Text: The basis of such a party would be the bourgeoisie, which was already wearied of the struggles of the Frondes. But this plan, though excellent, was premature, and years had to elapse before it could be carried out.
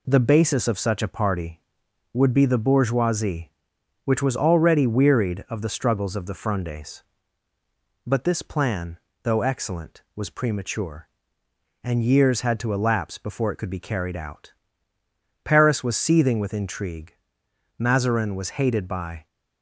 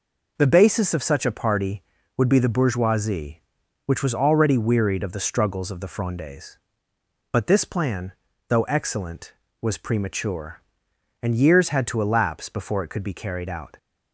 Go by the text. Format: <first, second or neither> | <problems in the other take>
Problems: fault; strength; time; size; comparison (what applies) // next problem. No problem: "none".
second | goes on to say "Paris was seething with intrigue Mazarin was hated by"; strong; from 15.4 s on; 3.8 s long